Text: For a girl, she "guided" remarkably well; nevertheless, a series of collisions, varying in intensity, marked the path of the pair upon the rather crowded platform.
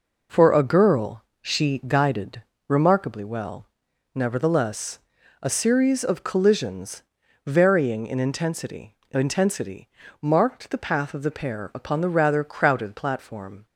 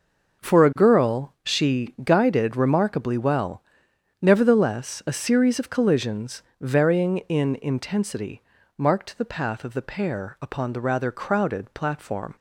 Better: second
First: pauses between "guided" and "remarkably"; slight; at 2.4 s; 0.26 s long // says "intensity" twice; at 9.1 s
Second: none

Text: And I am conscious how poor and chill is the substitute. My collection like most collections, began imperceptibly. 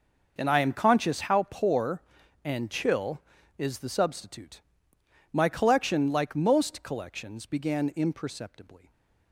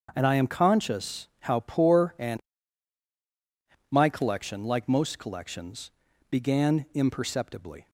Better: first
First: none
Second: starts louder than the rest; until 1.1 s; 7 dB // skips "chill is the substitute"; at 3.1 s

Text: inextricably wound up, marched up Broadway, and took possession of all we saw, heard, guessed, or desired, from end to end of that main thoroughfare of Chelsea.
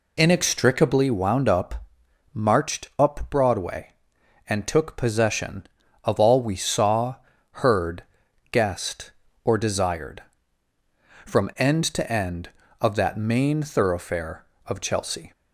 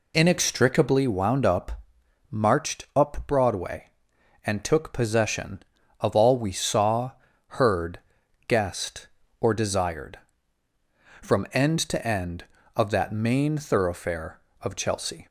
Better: neither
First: none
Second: none

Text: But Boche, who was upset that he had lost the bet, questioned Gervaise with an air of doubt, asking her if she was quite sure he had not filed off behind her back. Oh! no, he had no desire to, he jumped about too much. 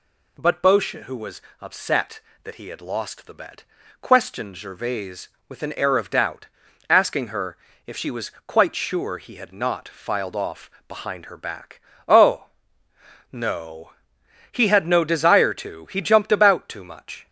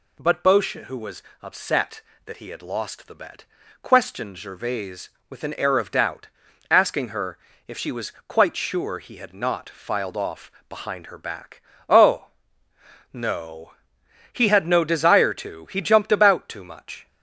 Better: neither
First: pauses between "was" and "upset"; slight; at 1.4 s; 0.20 s long // pauses between "her" and "if"; slight; at 7.5 s; 0.30 s long // pauses between "was" and "quite"; slight; at 8.3 s; 0.16 s long // pauses between "off" and "behind"; slight; at 10.7 s; 0.18 s long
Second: pauses between "was" and "upset"; slight; at 1.2 s; 0.20 s long // pauses between "her" and "if"; slight; at 7.3 s; 0.30 s long // pauses between "was" and "quite"; slight; at 8.1 s; 0.16 s long // pauses between "off" and "behind"; slight; at 10.5 s; 0.18 s long

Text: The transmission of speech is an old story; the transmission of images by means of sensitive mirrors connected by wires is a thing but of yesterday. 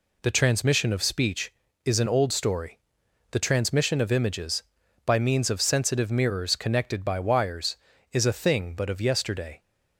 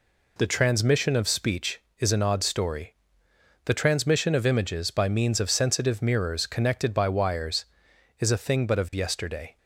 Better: first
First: none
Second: says "odd" for "old"; at 2.2 s

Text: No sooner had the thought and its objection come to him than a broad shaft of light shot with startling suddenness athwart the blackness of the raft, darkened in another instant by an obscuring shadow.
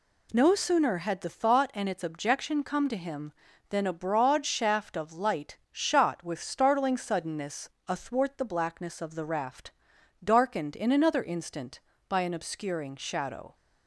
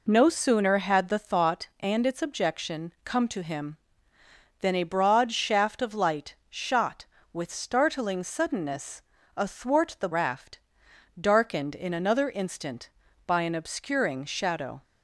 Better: first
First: pauses between "suddenness" and "athwart"; slight; at 7.7 s; 0.16 s long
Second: pauses between "light" and "shot"; slight; at 6.3 s; 0.16 s long // pauses between "suddenness" and "athwart"; slight; at 9.0 s; 0.34 s long // skips "blackness of the"; at 10.1 s

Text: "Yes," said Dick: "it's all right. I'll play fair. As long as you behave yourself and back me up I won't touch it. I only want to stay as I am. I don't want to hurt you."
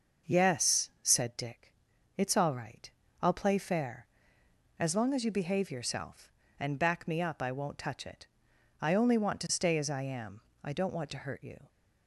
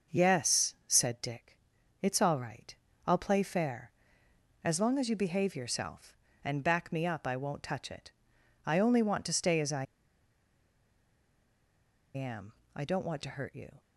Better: first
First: starts louder than the rest; until 1.3 s; 6 dB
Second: starts louder than the rest; noticeable; until 1.2 s; 6 dB // pauses between "I" and "am"; strong; at 9.8 s; 2.3 s long

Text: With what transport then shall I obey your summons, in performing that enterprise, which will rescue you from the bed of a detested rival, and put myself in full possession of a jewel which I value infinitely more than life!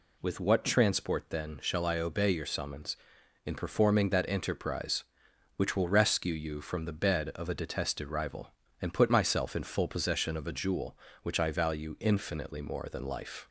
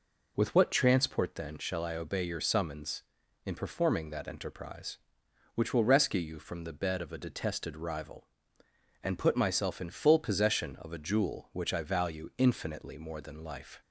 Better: neither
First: none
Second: none

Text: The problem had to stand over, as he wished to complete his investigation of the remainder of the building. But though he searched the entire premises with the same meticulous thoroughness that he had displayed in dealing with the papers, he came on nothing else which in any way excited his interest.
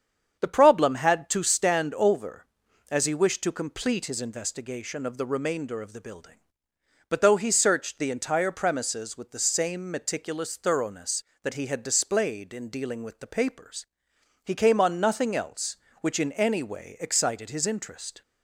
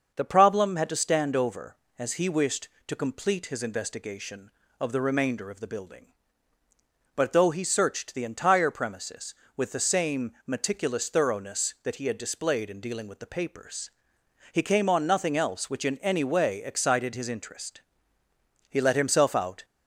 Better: first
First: starts louder than the rest; strong; until 1.4 s; 7.5 dB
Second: starts louder than the rest; until 1.1 s; 6 dB // goes on to say "He let himself out"; noticeable; from 18.6 s on; 0.96 s long

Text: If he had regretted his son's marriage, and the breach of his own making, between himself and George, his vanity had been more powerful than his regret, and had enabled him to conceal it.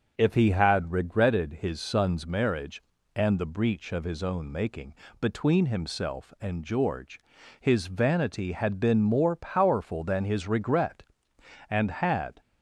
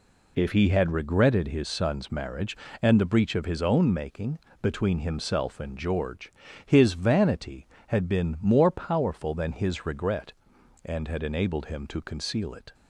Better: second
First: starts louder than the rest; until 1.1 s; 6.5 dB // stops before "enabled him to conceal it"; at 12.3 s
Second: none

